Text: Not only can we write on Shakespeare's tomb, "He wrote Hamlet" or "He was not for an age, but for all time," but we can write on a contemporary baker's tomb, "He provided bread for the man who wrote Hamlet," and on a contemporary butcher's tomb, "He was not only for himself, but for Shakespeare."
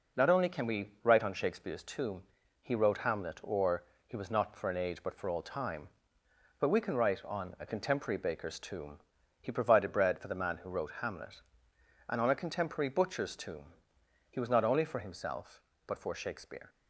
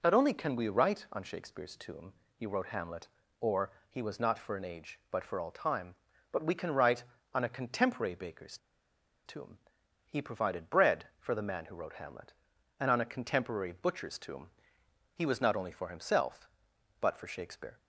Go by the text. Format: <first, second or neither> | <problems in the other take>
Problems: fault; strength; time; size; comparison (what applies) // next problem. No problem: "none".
first | pauses between "or" and "He"; slight; at 3.7 s; 0.20 s long; slight in the first // pauses between "baker's" and "tomb"; noticeable; at 8.5 s; 0.69 s long